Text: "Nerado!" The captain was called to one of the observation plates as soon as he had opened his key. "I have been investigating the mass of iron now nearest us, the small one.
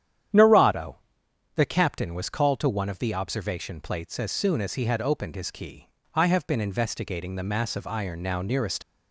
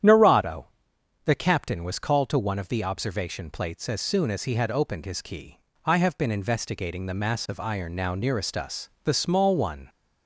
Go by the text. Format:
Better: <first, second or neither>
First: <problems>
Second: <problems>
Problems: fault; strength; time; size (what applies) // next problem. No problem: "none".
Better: second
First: starts louder than the rest; strong; until 1.9 s; 10 dB // stops before "us the small one"; at 8.8 s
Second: starts louder than the rest; strong; until 1.6 s; 10 dB